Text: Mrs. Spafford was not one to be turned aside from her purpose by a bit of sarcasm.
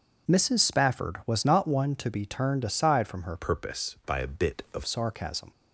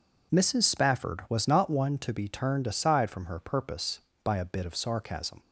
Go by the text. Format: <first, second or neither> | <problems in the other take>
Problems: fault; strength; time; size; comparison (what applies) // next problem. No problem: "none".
second | changes voice from "purpose" to "of"; from 3.3 to 4.8 s; 1.5 s long